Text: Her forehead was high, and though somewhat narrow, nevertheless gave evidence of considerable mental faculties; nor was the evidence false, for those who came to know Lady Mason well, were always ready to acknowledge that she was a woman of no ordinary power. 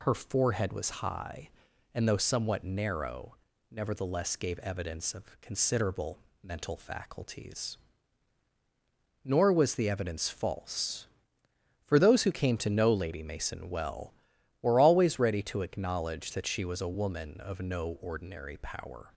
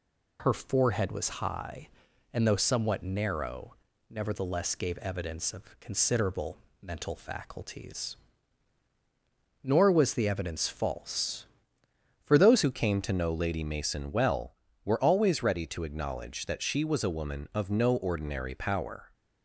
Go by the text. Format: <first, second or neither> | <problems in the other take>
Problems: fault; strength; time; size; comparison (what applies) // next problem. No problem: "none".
first | pauses between "considerable" and "mental"; slight; at 6.5 s; 0.24 s long; slight in the first // changes voice at "who"; from 12.6 s on; 6.5 s long